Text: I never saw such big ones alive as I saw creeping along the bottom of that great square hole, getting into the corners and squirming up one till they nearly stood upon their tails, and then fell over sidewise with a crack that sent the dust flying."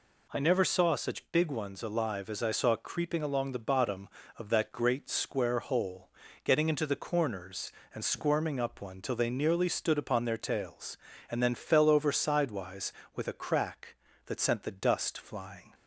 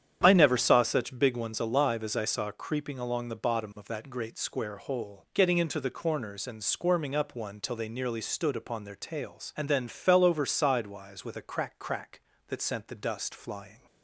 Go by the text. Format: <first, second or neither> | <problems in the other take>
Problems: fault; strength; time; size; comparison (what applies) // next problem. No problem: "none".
first | starts louder than the rest; strong; until 1.2 s; 9 dB // says "crack" twice; at 11.7 s